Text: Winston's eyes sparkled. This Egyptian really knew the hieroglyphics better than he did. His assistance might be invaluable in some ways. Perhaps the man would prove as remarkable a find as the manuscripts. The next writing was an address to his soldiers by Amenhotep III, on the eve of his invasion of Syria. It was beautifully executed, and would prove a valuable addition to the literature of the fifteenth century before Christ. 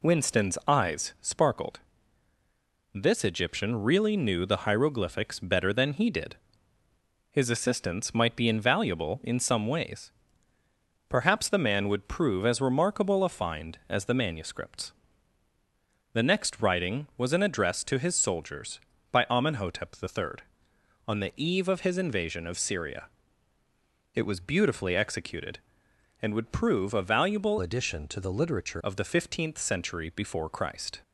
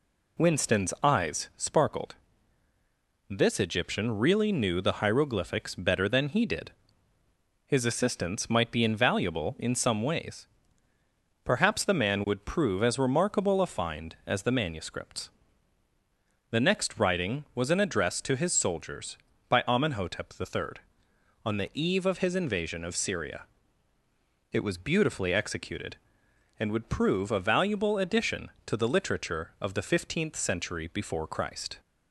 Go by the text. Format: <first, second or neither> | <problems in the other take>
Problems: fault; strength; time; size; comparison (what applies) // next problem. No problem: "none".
second | changes voice from "addition" to "literature"; from 27.6 to 28.8 s; 1.2 s long